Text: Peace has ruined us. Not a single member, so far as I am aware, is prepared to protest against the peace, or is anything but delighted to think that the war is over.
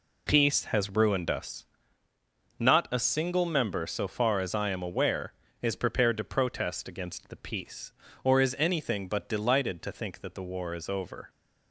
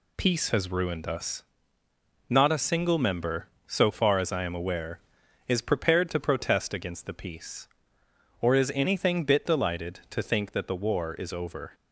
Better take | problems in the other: first | says "bit" for "but"; at 9.2 s

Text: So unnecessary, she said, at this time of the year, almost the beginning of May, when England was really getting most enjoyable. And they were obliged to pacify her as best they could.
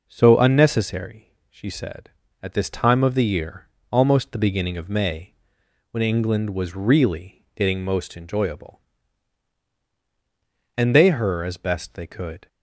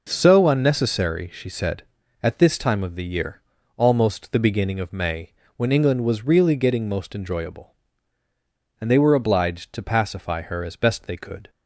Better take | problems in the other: second | skips "were obliged to pacify"; at 11.0 s

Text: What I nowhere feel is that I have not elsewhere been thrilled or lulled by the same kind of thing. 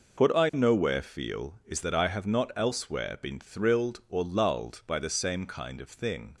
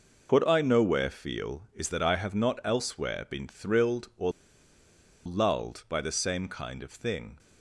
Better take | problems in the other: first | pauses between "or" and "lulled"; noticeable; at 4.3 s; 0.95 s long

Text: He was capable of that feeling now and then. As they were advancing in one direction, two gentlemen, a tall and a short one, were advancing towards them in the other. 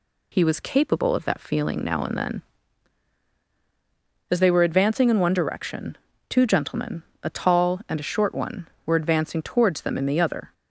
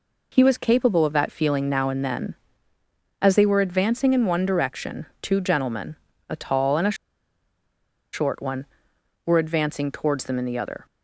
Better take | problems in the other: first | pauses between "a" and "short"; at 6.9 s; 1.1 s long

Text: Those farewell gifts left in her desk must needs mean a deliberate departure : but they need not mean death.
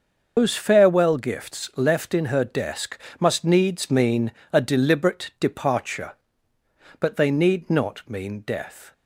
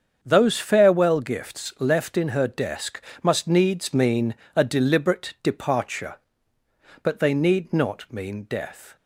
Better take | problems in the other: second | loses the start of "Those"; at 0.3 s; 165 ms // starts louder than the rest; until 1.3 s; 6 dB; also in the second // pauses between "desk" and "must"; slight; at 2.9 s; 0.22 s long; slight in the second // pauses between "mean" and "a"; slight; at 4.3 s; 0.18 s long; slight in the second

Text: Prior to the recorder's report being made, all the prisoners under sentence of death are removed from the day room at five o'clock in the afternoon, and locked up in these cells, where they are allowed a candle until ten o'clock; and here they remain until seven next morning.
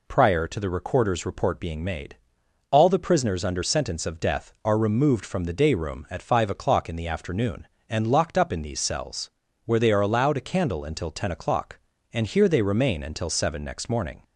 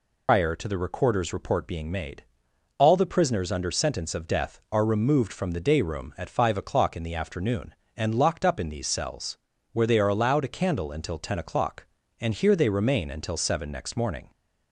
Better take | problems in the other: first | loses the start of "Prior"; at 0.2 s; 125 ms

